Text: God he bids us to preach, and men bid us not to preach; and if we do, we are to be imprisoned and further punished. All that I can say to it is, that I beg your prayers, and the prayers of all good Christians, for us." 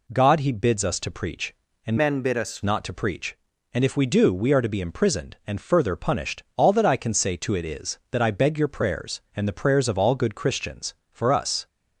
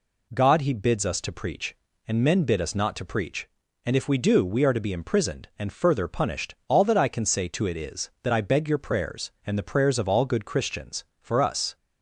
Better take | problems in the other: second | changes voice from "men" to "us"; from 1.9 to 2.6 s; 0.7 s long

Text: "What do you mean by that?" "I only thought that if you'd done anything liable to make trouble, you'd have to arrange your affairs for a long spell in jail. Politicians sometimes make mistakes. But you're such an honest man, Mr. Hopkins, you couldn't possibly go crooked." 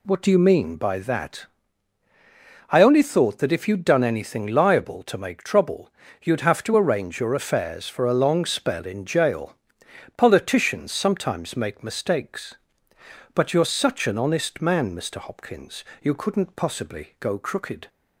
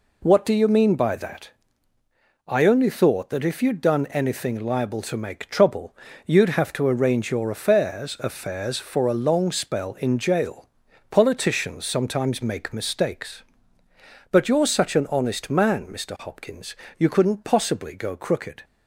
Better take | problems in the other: first | says "affairs" twice; at 8.2 s

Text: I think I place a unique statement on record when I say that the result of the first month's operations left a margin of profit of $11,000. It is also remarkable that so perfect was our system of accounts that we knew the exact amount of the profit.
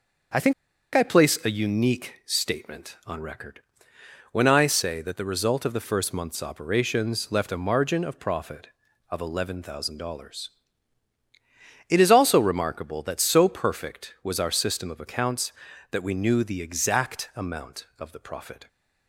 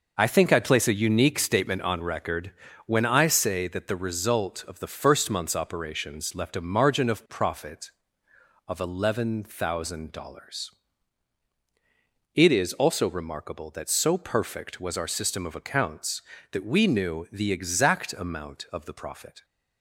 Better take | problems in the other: second | starts louder than the rest; noticeable; until 1.8 s; 6 dB // pauses between "think" and "I"; at 0.5 s; 0.42 s long // pauses between "record" and "when"; noticeable; at 3.5 s; 0.72 s long; slight in the second

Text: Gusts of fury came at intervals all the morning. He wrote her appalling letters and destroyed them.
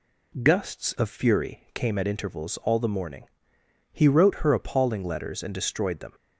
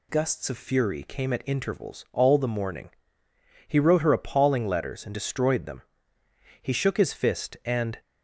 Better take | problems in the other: first | goes on to say "He shook his fist and"; from 6.6 s on; 1.3 s long

